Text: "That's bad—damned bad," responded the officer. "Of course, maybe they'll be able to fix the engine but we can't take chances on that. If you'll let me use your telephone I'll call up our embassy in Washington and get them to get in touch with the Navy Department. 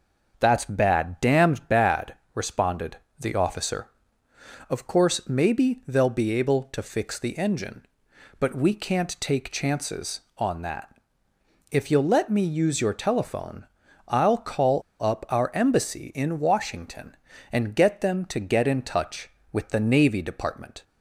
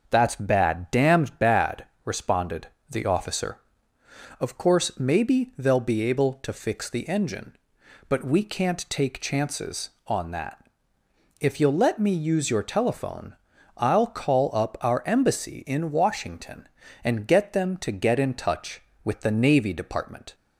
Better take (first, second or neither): second